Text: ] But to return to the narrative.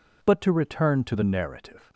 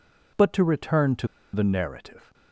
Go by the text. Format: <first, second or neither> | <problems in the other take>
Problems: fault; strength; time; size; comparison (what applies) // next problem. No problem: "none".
first | pauses between "to" and "the"; slight; at 1.2 s; 0.26 s long